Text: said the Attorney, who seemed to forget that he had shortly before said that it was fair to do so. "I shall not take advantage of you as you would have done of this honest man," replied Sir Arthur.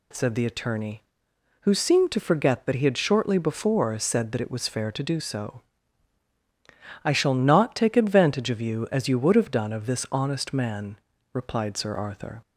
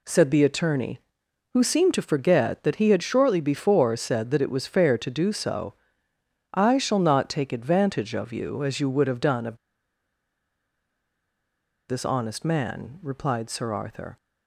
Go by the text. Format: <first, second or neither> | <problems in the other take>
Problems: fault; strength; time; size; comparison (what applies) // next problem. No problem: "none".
first | pauses between "of" and "this"; strong; at 9.5 s; 2.3 s long